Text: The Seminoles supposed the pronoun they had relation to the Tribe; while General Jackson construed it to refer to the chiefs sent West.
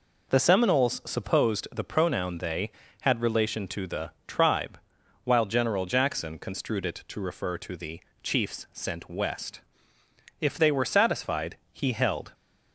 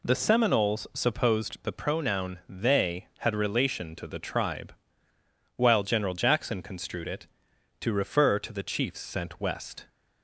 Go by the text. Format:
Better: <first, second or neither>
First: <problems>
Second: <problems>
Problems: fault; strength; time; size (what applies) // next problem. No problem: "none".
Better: second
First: pauses between "the" and "Tribe"; slight; at 4.1 s; 0.16 s long // pauses between "the" and "chiefs"; slight; at 7.9 s; 0.22 s long // goes on to say "If they were satisfied he held"; strong; from 10.3 s on; 1.9 s long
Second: none